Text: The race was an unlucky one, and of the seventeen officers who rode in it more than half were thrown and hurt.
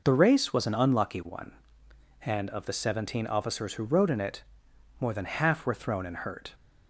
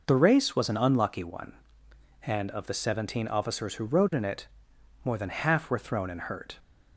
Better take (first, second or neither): neither